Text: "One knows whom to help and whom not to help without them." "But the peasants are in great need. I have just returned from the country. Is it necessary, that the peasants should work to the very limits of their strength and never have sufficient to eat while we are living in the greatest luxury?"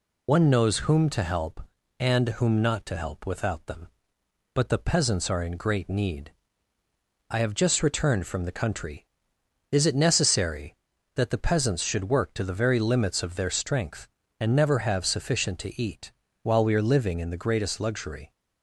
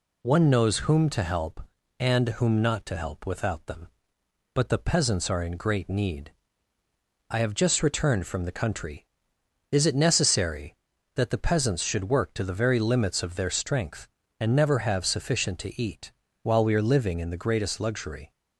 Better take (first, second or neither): second